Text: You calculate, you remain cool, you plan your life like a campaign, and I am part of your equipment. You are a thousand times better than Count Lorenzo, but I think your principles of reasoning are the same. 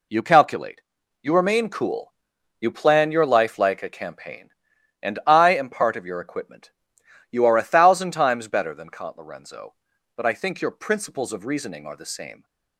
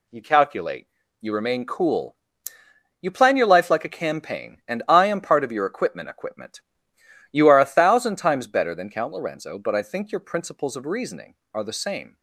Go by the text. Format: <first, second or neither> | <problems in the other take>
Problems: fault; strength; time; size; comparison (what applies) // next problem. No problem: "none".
first | says "equipment" twice; at 6.0 s